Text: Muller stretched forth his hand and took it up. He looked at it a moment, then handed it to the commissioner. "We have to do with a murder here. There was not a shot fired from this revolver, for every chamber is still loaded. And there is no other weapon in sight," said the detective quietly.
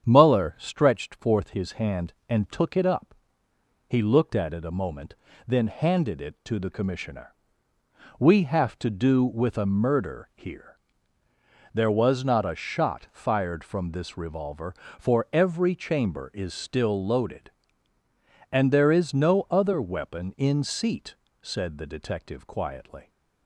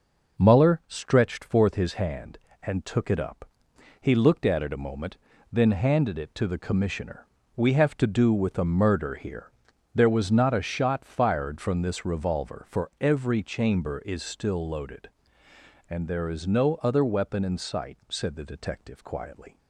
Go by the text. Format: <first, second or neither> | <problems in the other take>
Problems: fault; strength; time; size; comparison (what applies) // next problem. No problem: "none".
second | starts louder than the rest; strong; until 1.0 s; 8 dB // says "seat" for "sight"; at 20.6 s